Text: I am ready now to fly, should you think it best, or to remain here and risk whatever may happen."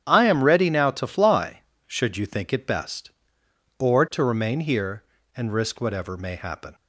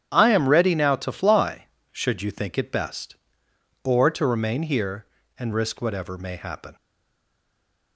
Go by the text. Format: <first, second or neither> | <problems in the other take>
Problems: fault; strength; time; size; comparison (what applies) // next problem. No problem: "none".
first | starts louder than the rest; strong; until 1.1 s; 10 dB; strong in the first // stays silent after the last word; noticeable; from 6.7 s on; 1.2 s long